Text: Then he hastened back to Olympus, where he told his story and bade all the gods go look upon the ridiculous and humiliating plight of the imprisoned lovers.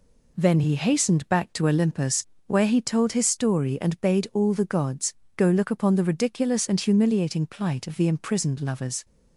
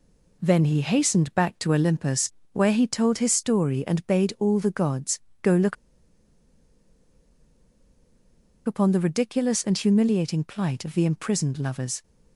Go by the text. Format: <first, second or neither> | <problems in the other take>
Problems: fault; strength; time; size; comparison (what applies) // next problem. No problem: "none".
first | pauses between "gods" and "go"; slight; at 5.1 s; 0.24 s long; slight in the first // pauses between "look" and "upon"; strong; at 5.7 s; 2.9 s long